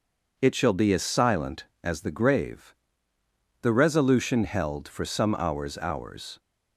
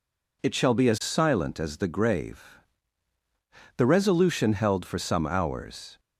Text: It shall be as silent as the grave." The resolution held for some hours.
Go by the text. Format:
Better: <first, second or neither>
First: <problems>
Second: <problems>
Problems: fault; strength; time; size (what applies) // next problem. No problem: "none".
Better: second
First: says "hours" twice; at 5.7 s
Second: none